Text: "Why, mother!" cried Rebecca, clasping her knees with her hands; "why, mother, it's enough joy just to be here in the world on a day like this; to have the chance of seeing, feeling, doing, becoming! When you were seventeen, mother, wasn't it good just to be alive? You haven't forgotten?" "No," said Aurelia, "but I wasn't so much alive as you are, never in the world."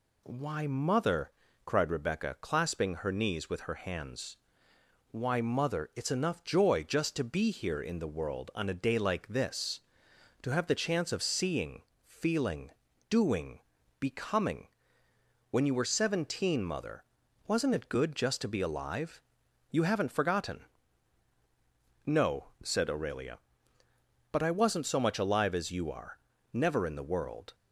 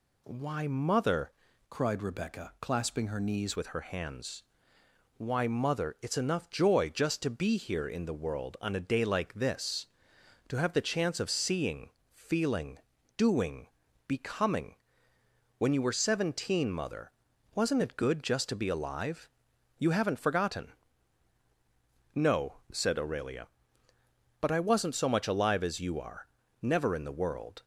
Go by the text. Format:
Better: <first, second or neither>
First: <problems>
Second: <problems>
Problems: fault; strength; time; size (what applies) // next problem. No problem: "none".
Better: first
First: none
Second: changes voice from "cried" to "knees"; from 1.7 to 3.5 s; 1.8 s long